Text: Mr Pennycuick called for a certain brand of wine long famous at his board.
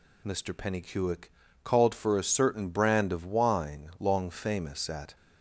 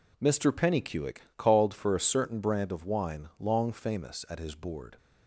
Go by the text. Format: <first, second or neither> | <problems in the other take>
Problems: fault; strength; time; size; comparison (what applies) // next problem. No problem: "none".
second | pauses between "Pennycuick" and "called"; slight; at 1.3 s; 0.32 s long; slight in the second // stops before "his board"; at 5.1 s